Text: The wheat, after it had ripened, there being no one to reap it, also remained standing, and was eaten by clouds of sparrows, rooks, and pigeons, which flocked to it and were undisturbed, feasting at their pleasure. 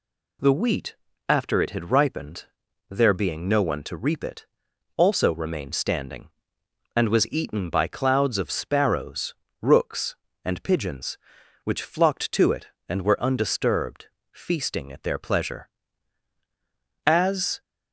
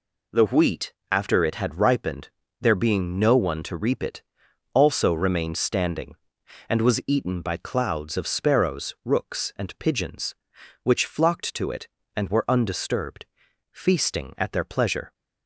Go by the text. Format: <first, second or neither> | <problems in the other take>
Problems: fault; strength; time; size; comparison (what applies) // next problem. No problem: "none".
second | goes on to say "As"; from 17.0 s on; 0.54 s long